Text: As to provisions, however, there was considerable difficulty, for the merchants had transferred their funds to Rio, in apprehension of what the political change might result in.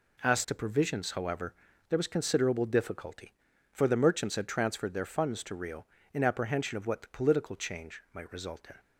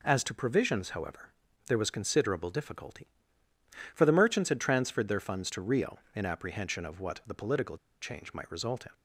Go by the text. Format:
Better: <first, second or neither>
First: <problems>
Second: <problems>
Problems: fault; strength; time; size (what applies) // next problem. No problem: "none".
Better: first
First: none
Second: pauses between "political" and "change"; slight; at 7.7 s; 0.25 s long